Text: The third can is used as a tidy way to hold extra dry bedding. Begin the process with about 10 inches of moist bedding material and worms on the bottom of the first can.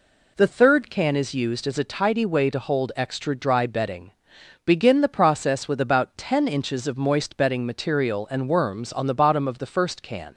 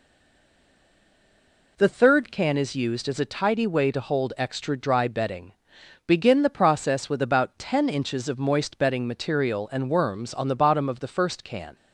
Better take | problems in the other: first | stays silent before the first word; noticeable; until 1.7 s; 1.7 s long

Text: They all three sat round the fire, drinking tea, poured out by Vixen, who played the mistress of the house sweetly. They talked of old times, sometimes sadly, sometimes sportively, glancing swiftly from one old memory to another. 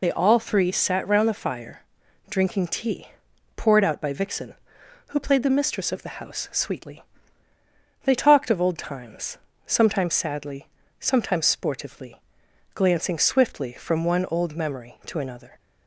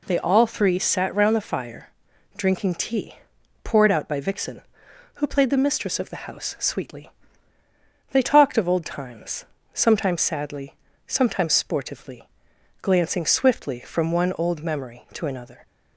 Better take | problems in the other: second | loses the start of "They"; at 0.0 s; 70 ms

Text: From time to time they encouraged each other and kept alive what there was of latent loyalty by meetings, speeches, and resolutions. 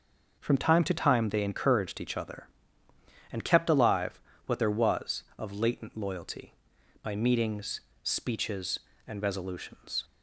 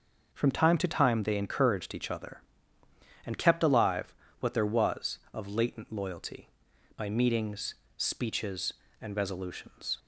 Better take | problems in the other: neither | starts louder than the rest; noticeable; the same in both // pauses between "alive" and "what"; slight; the same in both

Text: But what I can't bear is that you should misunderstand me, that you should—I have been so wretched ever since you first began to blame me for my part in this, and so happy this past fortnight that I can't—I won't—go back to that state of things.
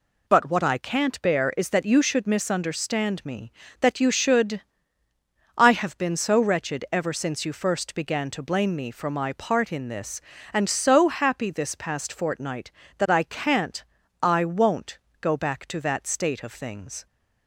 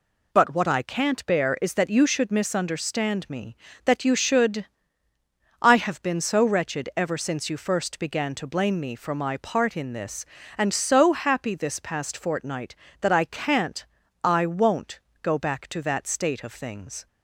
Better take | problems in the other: neither | none

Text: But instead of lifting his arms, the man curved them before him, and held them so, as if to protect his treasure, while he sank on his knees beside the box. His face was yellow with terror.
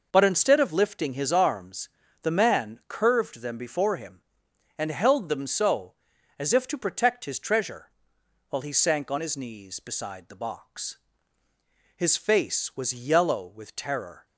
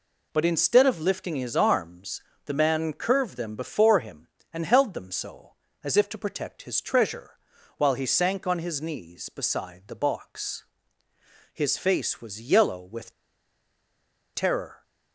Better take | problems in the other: first | pauses between "with" and "terror"; at 13.1 s; 1.2 s long

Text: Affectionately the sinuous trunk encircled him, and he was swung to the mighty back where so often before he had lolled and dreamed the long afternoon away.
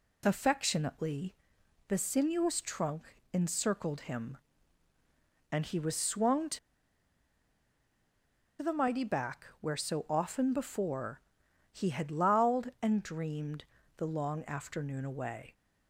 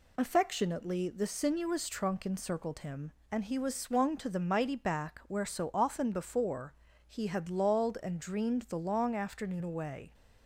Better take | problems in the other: second | pauses between "Affectionately" and "the"; noticeable; at 1.3 s; 0.54 s long // pauses between "trunk" and "encircled"; slight; at 3.1 s; 0.20 s long // pauses between "to" and "the"; strong; at 6.5 s; 2.0 s long // pauses between "before" and "he"; noticeable; at 11.1 s; 0.50 s long; slight in the second // pauses between "dreamed" and "the"; slight; at 13.6 s; 0.32 s long

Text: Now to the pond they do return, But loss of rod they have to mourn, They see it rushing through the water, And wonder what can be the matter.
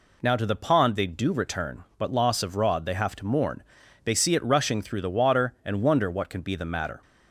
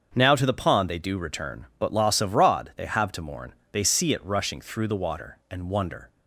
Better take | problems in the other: first | starts louder than the rest; until 1.1 s; 7 dB // stops before "what can be the matter"; at 6.0 s

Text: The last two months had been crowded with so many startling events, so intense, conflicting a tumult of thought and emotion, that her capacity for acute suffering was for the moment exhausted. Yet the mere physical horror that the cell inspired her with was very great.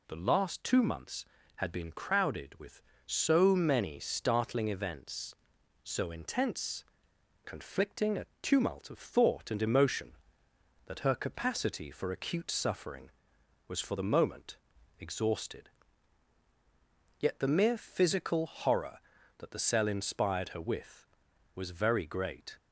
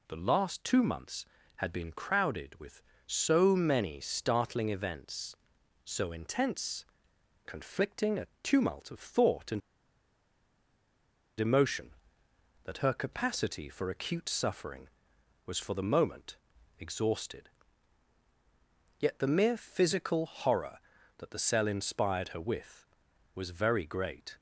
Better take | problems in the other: first | pauses between "a" and "tumult"; slight; at 8.2 s; 0.16 s long; slight in the first // pauses between "and" and "emotion"; strong; at 9.6 s; 1.8 s long // pauses between "moment" and "exhausted"; at 16.3 s; 0.42 s long; also in the first

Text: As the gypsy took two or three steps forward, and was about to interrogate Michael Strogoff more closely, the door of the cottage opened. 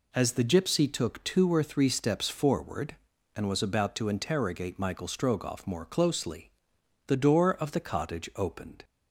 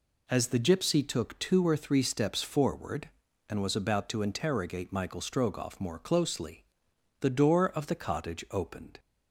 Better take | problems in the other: neither | none

